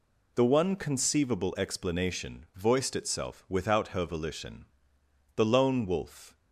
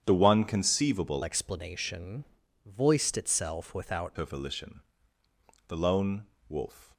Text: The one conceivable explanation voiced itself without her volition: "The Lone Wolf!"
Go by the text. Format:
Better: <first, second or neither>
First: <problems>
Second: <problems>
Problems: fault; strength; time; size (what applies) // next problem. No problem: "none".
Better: first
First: none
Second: starts louder than the rest; strong; until 1.0 s; 9 dB // changes voice from "explanation" to "without"; from 1.2 to 4.1 s; 2.9 s long // pauses between "explanation" and "voiced"; at 2.2 s; 0.40 s long // pauses between "Lone" and "Wolf"; slight; at 6.2 s; 0.20 s long